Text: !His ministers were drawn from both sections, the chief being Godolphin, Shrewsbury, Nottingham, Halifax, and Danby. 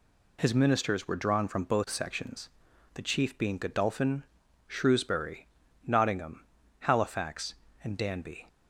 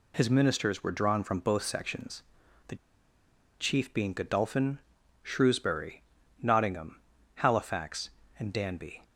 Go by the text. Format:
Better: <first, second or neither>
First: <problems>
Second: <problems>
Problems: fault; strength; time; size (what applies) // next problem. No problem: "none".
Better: first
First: none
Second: pauses between "the" and "chief"; noticeable; at 2.7 s; 0.84 s long